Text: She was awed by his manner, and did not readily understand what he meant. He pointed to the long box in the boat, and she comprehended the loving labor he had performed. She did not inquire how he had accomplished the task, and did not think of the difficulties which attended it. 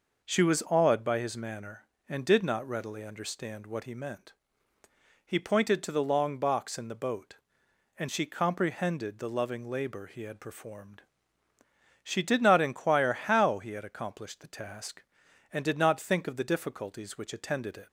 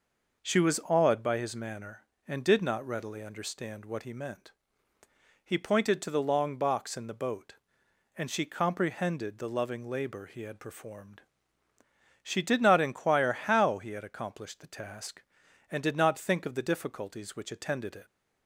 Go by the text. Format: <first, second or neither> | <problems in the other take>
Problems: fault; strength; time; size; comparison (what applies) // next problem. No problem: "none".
neither | none